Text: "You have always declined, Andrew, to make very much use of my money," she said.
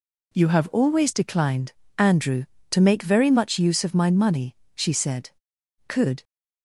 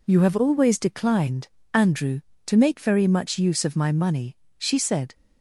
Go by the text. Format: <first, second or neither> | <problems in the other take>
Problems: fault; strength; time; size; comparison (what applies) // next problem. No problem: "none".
second | goes on to say "Could"; slight; from 5.8 s on; 0.34 s long